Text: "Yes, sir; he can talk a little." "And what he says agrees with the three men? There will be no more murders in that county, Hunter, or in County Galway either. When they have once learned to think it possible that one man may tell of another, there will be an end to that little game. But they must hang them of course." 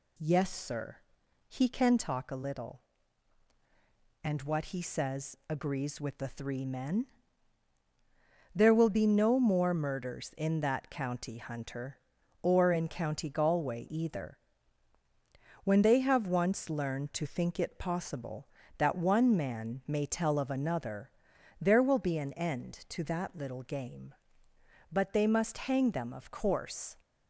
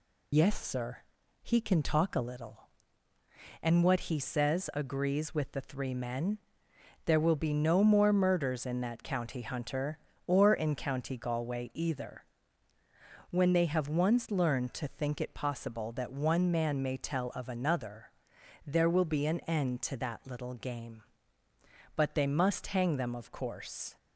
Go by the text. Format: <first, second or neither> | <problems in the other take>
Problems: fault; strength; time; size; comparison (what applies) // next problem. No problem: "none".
first | loses the start of "Yes"; at 0.3 s; 60 ms